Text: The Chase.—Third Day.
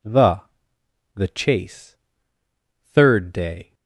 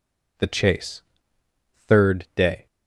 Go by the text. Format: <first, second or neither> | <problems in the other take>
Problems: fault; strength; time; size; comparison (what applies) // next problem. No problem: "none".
second | says "The" twice; at 1.1 s